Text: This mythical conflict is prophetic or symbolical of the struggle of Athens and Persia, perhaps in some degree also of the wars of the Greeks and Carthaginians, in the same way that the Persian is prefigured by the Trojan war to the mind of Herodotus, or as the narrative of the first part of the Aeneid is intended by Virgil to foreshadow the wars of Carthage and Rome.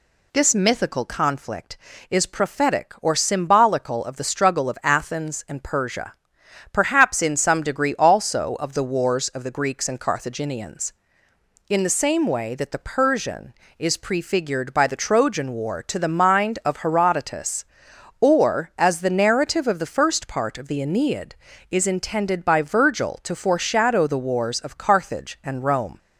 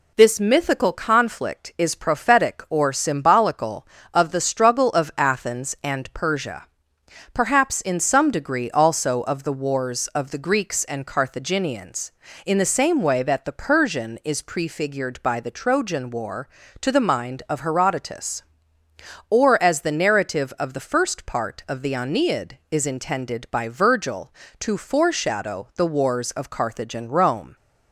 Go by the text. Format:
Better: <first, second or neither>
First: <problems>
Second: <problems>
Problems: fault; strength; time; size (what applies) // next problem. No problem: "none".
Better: neither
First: none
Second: none